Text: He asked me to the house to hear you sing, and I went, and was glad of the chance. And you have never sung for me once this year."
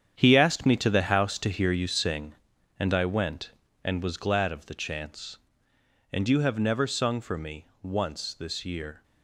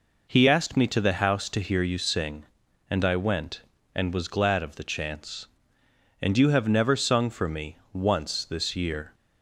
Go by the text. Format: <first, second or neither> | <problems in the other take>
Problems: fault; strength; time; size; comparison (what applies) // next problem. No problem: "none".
second | gets quieter; strong; throughout; 11 dB // pauses between "me" and "once"; slight; at 7.6 s; 0.16 s long; slight in the second